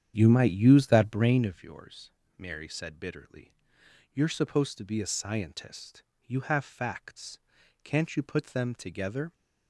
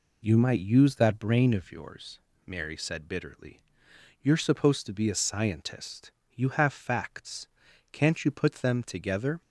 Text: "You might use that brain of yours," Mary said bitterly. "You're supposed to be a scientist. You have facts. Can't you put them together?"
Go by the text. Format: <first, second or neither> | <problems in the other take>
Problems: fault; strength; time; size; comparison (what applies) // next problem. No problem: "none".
second | starts louder than the rest; strong; until 1.5 s; 9 dB